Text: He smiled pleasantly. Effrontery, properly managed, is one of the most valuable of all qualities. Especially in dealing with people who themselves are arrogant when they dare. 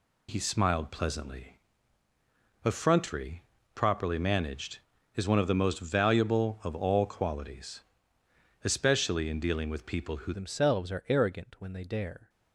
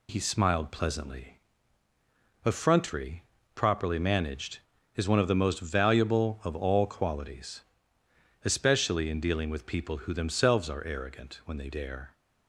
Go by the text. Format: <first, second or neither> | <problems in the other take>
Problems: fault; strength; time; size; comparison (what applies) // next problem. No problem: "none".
second | changes voice at "themselves"; from 10.3 s on; 1.9 s long